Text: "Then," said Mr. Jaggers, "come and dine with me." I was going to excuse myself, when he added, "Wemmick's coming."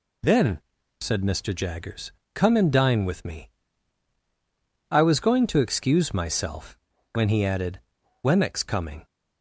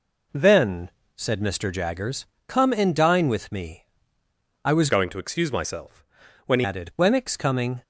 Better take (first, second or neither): first